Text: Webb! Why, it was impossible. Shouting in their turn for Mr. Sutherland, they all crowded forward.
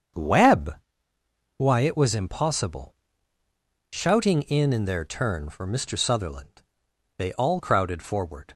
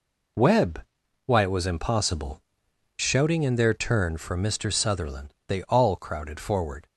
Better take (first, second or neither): second